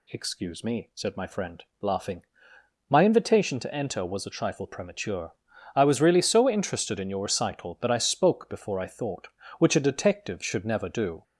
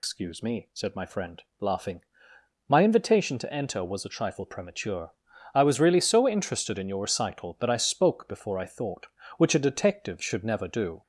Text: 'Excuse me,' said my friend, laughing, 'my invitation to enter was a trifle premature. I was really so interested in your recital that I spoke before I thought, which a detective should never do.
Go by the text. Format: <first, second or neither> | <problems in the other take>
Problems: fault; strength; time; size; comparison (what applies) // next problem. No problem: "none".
first | loses the start of "Excuse"; at 0.0 s; 150 ms